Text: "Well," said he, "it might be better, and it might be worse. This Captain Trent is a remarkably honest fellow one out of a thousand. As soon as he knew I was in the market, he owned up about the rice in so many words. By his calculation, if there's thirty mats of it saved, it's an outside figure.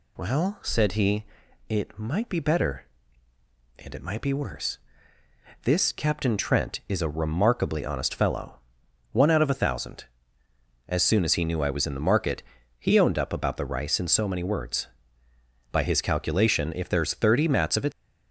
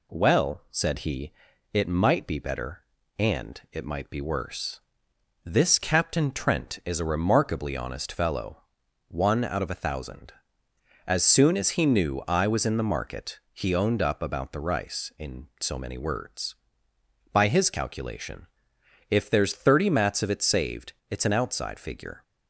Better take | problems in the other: second | pauses between "fellow" and "one"; noticeable; at 8.5 s; 0.54 s long; also in the second // stops before "saved it's an outside figure"; at 17.9 s

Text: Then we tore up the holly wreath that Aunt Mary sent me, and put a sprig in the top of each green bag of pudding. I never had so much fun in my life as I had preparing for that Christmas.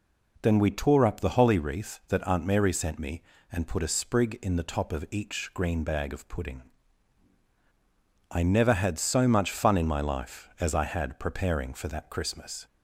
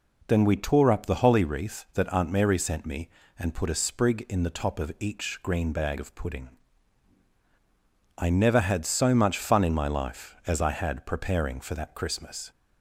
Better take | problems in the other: neither | none

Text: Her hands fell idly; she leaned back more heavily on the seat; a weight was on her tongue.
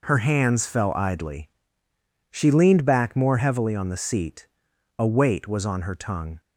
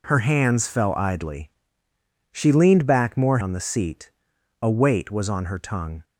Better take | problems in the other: first | skips "heavily"; at 3.3 s

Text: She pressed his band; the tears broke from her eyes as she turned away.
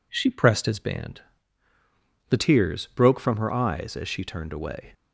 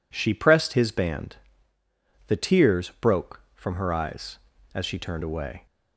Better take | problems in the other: neither | none

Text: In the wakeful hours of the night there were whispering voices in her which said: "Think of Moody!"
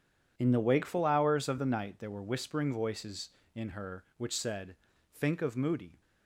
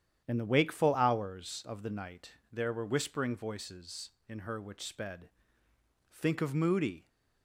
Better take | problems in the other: first | starts louder than the rest; strong; until 1.2 s; 9.5 dB // pauses between "night" and "there"; slight; at 2.3 s; 0.18 s long // says "sped" for "said"; at 4.8 s

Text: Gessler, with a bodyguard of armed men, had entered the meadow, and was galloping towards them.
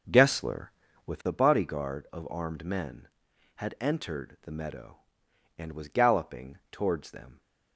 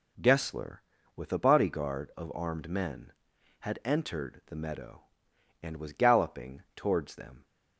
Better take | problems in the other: second | starts louder than the rest; until 1.3 s; 7 dB

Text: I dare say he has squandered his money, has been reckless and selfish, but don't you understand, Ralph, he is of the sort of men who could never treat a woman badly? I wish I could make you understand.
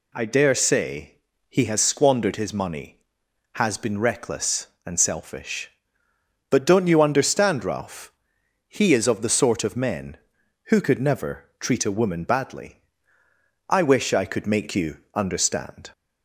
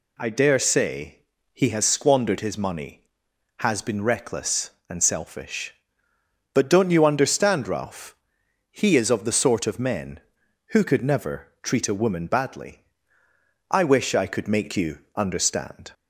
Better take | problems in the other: neither | pauses between "say" and "he"; slight; the same in both // pauses between "you" and "understand"; slight; the same in both

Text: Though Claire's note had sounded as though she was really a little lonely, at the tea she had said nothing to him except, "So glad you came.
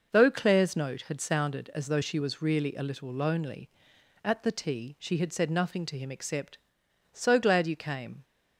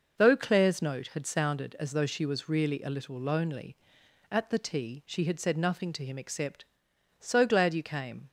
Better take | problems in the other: neither | none

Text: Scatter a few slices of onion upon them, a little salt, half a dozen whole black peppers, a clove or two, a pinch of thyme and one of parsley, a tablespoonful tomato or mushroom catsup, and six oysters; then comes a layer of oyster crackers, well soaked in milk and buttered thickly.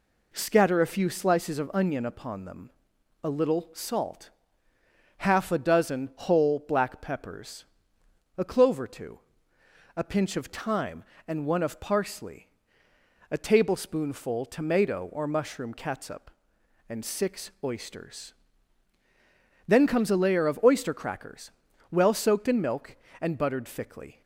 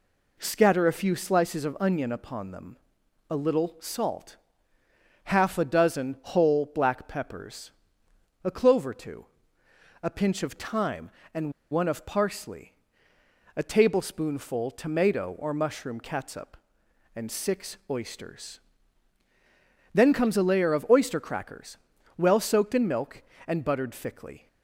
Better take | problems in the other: first | pauses between "and" and "one"; slight; at 11.5 s; 0.19 s long

